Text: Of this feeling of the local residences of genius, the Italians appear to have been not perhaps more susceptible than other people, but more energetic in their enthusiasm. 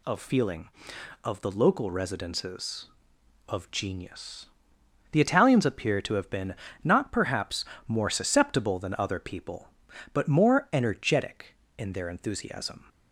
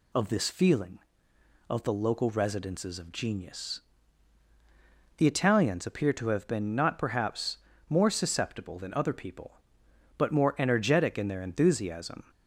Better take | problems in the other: second | skips "this"; at 0.1 s // pauses between "been" and "not"; slight; at 6.5 s; 0.28 s long // pauses between "perhaps" and "more"; slight; at 7.6 s; 0.24 s long; slight in the second

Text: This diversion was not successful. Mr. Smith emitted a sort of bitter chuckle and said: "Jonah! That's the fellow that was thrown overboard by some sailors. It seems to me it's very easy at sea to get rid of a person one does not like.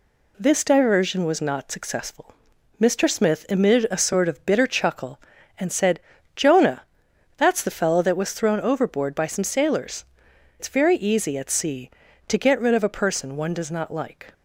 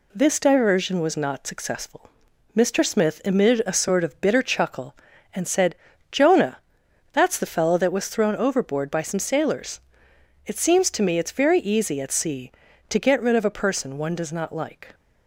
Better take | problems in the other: second | skips "It seems to me"; at 10.3 s

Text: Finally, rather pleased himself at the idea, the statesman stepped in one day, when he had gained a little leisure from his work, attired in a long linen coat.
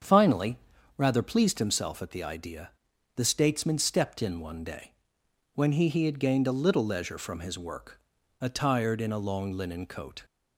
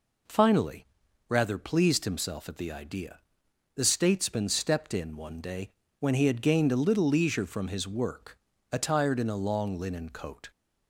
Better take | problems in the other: second | starts louder than the rest; strong; until 1.4 s; 7.5 dB // says "he" twice; at 5.8 s

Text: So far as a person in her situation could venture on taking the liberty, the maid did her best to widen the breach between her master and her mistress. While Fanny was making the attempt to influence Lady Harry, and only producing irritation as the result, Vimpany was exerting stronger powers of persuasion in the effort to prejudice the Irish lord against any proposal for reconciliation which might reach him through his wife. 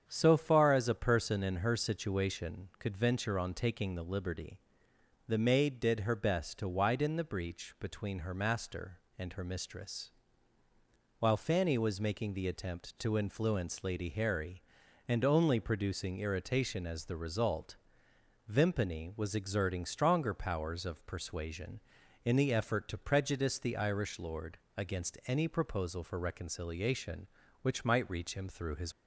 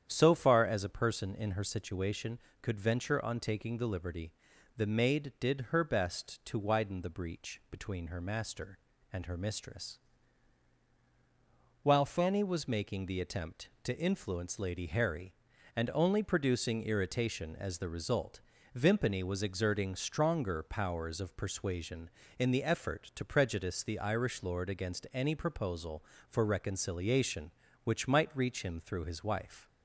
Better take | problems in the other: second | starts louder than the rest; strong; until 1.0 s; 8 dB; strong in the second // pauses between "lord" and "against"; slight; at 24.5 s; 0.18 s long // stops before "wife"; at 28.9 s

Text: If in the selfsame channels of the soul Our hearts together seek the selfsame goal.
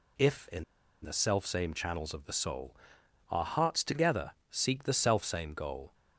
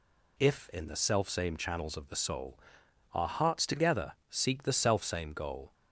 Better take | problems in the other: second | pauses between "in" and "the"; at 0.6 s; 0.39 s long // pauses between "soul" and "Our"; noticeable; at 2.7 s; 0.54 s long; noticeable in the second // pauses between "together" and "seek"; slight; at 4.3 s; 0.18 s long; slight in the second

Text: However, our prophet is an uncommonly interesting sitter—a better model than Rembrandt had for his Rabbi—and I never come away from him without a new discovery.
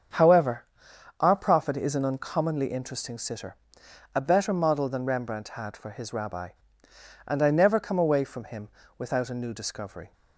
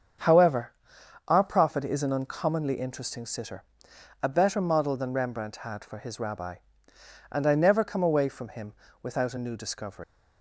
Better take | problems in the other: first | starts louder than the rest; until 1.7 s; 7 dB; strong in the first // pauses between "him" and "without"; slight; at 8.7 s; 0.28 s long; slight in the first // leaves "discovery" unfinished; at 10.0 s; 110 ms

